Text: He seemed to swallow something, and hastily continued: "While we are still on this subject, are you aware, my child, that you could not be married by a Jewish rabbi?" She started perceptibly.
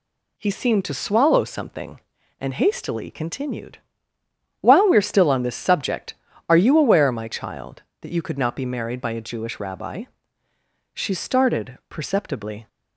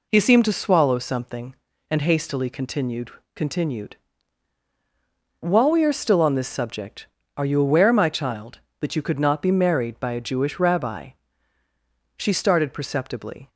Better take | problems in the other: first | says "continued" twice; at 3.3 s

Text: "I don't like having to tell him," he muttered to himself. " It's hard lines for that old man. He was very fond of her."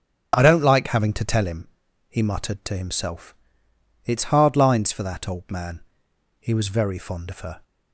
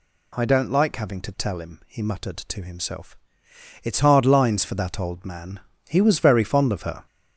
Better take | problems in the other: first | gets louder; noticeable; throughout; 4.5 dB

